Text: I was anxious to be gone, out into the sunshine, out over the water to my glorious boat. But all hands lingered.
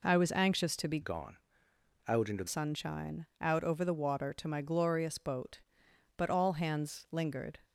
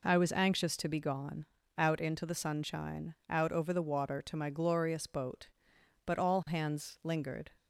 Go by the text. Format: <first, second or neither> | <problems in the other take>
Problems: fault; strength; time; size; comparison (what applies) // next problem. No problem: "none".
second | changes voice from "gone" to "the"; from 1.0 to 2.4 s; 1.4 s long